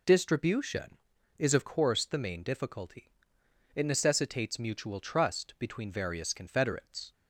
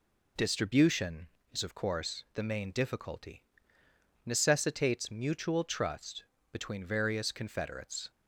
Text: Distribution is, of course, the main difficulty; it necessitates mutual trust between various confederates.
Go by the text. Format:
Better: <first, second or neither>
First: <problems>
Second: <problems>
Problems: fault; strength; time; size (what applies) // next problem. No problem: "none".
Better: first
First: none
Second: skips "it"; at 3.8 s // pauses between "trust" and "between"; slight; at 6.2 s; 0.28 s long